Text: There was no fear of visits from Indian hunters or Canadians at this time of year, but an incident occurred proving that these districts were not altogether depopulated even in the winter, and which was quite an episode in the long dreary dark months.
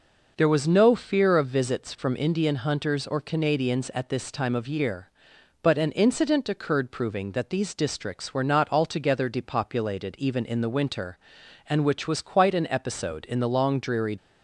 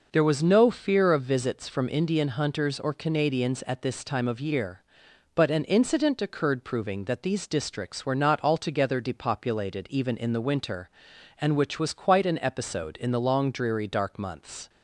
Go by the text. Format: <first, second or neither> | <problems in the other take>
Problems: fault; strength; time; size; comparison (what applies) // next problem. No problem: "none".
second | stops before "dark months"; at 14.1 s